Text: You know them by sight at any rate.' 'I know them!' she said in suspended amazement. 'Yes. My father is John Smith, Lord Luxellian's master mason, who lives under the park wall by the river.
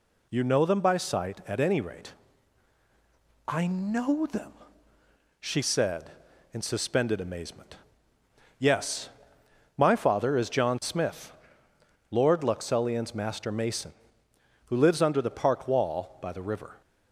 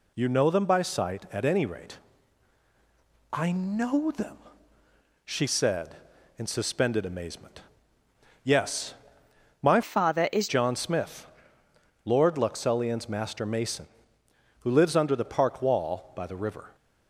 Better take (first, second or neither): first